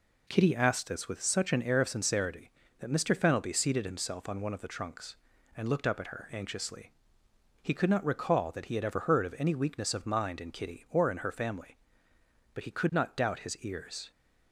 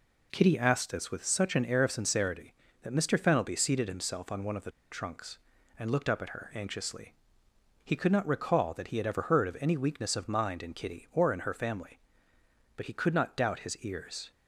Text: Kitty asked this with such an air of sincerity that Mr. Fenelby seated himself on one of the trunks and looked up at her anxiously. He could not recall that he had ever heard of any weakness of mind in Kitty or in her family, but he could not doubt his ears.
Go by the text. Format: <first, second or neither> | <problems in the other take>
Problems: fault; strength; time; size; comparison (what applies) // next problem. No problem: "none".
first | pauses between "the" and "trunks"; slight; at 4.6 s; 0.20 s long